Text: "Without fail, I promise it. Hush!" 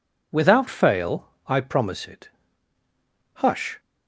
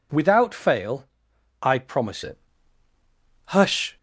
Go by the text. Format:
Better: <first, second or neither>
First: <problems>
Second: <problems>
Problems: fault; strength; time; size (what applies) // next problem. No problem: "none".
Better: first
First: none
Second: changes voice at "it"; from 2.2 s on; 1.7 s long